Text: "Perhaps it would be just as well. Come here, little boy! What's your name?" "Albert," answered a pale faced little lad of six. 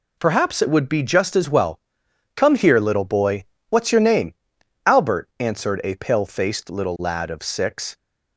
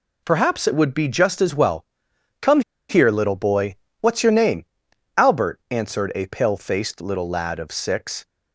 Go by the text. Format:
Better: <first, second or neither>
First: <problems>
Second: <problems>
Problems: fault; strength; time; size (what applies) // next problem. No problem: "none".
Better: first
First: none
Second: pauses between "Come" and "here"; slight; at 2.6 s; 0.28 s long